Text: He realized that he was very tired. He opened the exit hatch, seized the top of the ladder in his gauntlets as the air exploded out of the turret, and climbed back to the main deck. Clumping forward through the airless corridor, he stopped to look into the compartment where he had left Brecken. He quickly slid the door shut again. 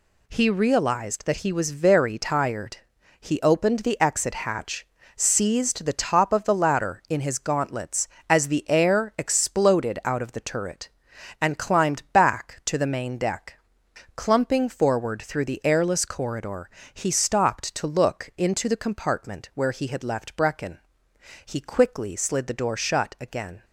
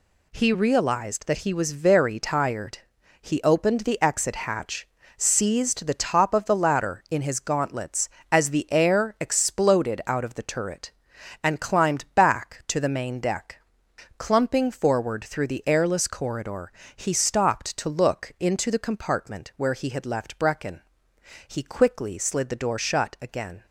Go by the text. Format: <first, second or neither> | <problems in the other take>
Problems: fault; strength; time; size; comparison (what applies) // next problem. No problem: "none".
neither | none